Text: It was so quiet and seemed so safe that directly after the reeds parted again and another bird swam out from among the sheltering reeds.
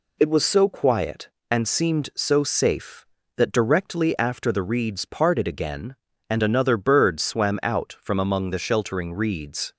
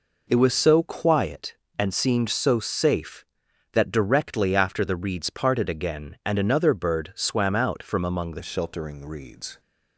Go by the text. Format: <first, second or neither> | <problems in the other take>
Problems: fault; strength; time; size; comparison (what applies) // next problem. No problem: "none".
first | changes voice at "sheltering"; from 8.4 s on; 1.1 s long